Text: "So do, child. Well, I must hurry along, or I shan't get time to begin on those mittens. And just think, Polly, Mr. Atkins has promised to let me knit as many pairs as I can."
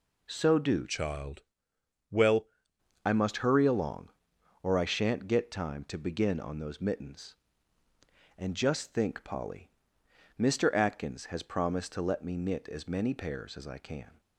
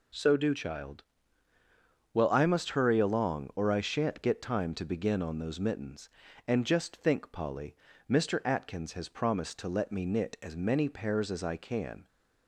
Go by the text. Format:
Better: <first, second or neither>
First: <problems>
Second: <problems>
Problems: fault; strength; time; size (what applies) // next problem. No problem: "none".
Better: second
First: changes voice from "child" to "Well"; from 0.8 to 2.4 s; 1.6 s long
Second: none